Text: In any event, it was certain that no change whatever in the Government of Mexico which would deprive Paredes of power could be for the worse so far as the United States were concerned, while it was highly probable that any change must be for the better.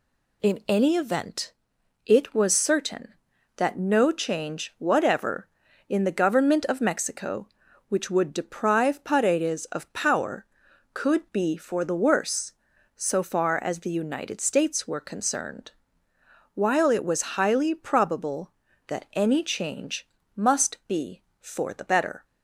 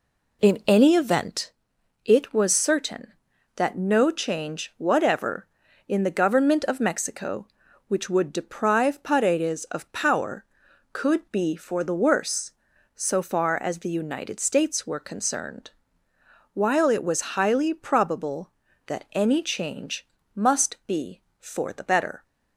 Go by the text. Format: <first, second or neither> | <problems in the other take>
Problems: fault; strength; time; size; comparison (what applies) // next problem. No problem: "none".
first | starts louder than the rest; slight; until 1.4 s; 3 dB // pauses between "change" and "must"; slight; at 20.0 s; 0.28 s long; slight in the first